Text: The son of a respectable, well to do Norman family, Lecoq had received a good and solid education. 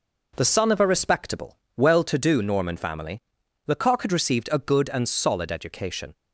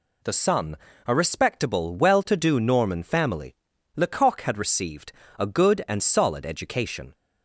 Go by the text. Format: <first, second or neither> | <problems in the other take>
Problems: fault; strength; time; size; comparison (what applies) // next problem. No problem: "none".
first | skips "of"; at 0.9 s // pauses between "received" and "a"; slight; at 5.1 s; 0.26 s long